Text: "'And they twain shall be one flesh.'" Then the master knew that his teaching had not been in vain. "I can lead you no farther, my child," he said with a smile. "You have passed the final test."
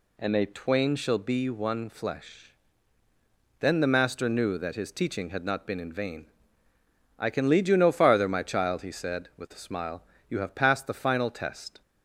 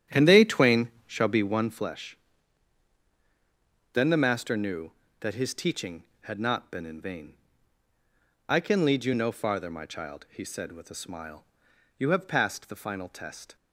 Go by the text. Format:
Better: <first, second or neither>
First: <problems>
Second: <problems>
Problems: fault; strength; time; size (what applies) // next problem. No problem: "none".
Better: first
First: none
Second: starts louder than the rest; strong; until 1.9 s; 10 dB // pauses between "twain" and "shall"; slight; at 0.8 s; 0.18 s long